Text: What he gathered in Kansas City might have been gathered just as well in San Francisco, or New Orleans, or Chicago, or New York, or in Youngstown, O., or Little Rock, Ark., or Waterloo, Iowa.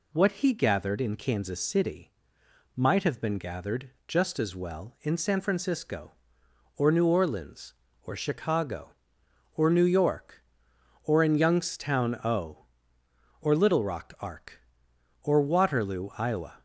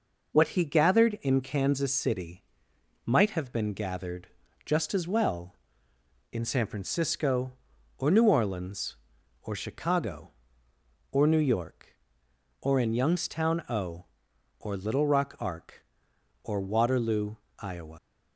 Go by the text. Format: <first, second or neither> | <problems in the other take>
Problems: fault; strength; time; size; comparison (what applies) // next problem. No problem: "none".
first | pauses between "City" and "might"; noticeable; at 2.4 s; 0.62 s long; noticeable in the first // pauses between "gathered" and "just"; at 4.2 s; 0.38 s long // leaves "Iowa" unfinished; at 17.9 s; 110 ms